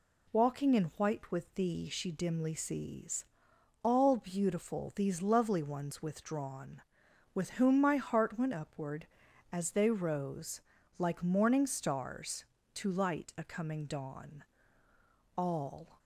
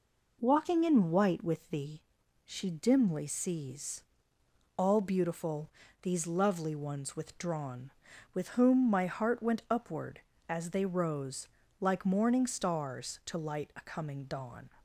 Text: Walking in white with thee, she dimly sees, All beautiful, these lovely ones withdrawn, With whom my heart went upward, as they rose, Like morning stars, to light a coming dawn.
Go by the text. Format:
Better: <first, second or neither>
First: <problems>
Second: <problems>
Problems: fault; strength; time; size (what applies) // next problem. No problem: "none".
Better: second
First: goes on to say "All"; noticeable; from 15.3 s on; 0.64 s long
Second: none